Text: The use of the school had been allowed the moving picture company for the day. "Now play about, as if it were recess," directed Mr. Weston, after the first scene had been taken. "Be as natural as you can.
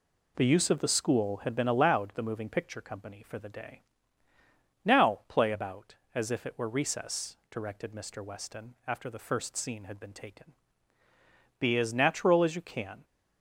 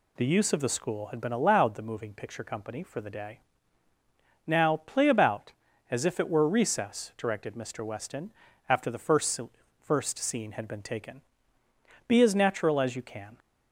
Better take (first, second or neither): first